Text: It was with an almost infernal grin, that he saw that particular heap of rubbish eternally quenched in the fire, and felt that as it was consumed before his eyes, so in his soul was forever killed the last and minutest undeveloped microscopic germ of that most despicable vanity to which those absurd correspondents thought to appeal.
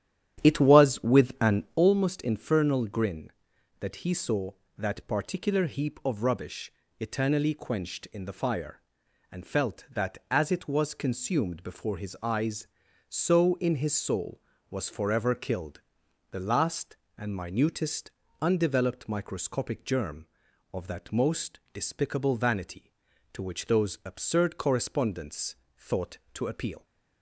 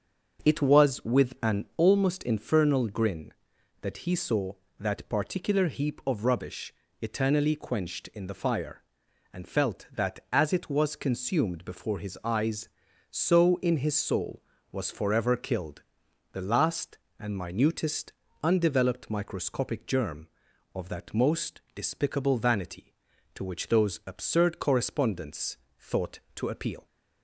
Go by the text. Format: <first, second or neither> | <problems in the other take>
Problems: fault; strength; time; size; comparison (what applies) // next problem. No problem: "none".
second | starts louder than the rest; strong; until 1.9 s; 10 dB // pauses between "rubbish" and "eternally"; slight; at 6.7 s; 0.30 s long; slight in the second // pauses between "killed" and "the"; noticeable; at 15.8 s; 0.48 s long; noticeable in the second // pauses between "minutest" and "undeveloped"; slight; at 18.1 s; 0.28 s long; slight in the second // pauses between "correspondents" and "thought"; slight; at 25.5 s; 0.20 s long; slight in the second